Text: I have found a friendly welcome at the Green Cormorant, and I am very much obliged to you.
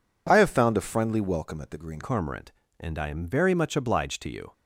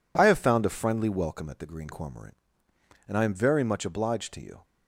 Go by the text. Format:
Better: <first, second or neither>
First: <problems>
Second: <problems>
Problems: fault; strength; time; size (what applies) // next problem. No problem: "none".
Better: second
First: changes voice at "Cormorant"; from 2.0 s on; 2.5 s long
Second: none